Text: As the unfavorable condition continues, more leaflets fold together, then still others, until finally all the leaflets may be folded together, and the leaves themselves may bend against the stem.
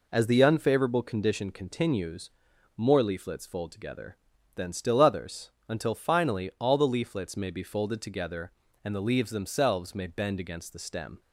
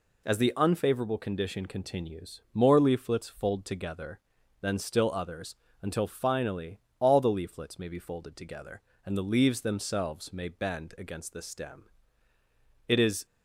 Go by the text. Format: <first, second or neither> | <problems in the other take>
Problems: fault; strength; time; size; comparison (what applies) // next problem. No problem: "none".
first | pauses between "finally" and "all"; slight; at 6.7 s; 0.20 s long // goes on to say "It is"; slight; from 12.8 s on; 0.38 s long